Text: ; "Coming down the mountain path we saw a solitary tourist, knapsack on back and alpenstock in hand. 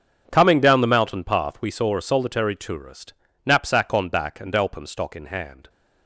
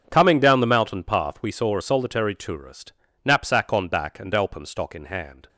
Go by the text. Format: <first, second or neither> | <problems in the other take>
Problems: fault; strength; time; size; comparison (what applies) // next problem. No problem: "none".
neither | starts louder than the rest; strong; the same in both